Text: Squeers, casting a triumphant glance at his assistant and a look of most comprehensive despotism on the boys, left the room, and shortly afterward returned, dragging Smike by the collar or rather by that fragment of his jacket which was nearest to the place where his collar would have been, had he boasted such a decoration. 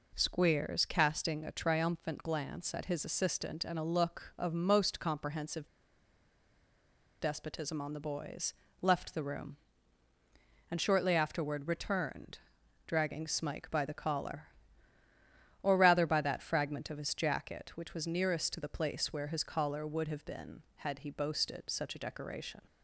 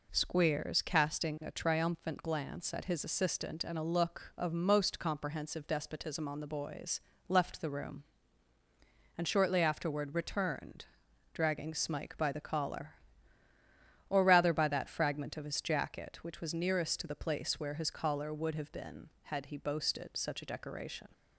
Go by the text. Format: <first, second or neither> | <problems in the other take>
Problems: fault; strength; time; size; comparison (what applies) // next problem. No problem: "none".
second | pauses between "comprehensive" and "despotism"; strong; at 5.6 s; 1.5 s long